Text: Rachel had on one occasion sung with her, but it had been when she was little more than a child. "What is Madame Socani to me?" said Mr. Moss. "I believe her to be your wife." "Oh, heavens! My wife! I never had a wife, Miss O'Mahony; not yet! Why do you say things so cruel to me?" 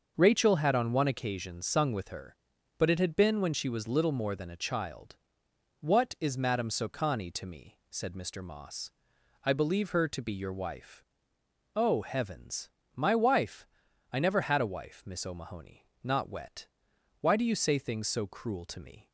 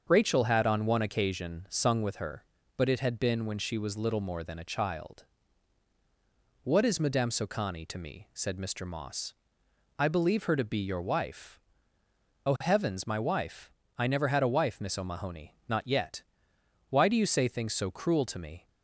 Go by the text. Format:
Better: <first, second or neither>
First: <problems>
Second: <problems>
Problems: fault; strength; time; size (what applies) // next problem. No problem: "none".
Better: second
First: starts louder than the rest; until 1.1 s; 6.5 dB // says "wet" for "yet"; at 16.2 s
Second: starts louder than the rest; until 1.0 s; 7 dB